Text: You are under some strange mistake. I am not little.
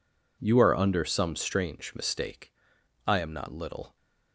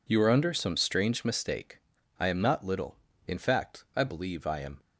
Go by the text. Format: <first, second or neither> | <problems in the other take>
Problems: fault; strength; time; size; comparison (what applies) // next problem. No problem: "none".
first | goes on to say "In fact I believe I am"; from 3.2 s on; 1.5 s long